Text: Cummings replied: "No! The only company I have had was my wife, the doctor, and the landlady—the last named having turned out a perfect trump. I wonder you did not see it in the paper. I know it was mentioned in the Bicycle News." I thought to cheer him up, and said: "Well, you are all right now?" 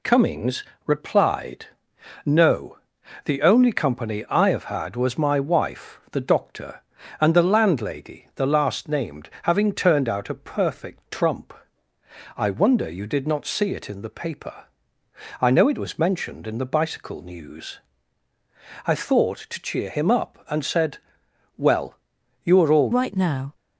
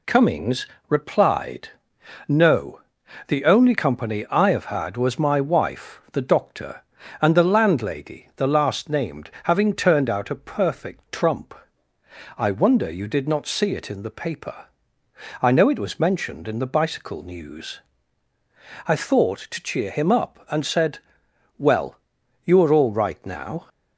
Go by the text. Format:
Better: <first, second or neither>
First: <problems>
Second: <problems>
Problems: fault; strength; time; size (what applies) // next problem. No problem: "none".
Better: second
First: pauses between "Cummings" and "replied"; slight; at 0.6 s; 0.22 s long // changes voice at "right"; from 22.9 s on; 0.6 s long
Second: pauses between "Cummings" and "replied"; slight; at 0.6 s; 0.22 s long